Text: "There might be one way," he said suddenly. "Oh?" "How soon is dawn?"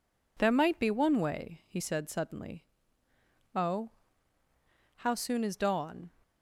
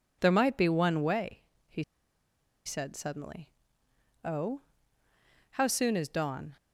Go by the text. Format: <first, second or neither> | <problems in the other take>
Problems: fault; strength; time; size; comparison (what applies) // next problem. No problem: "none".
first | pauses between "he" and "said"; noticeable; at 1.8 s; 0.83 s long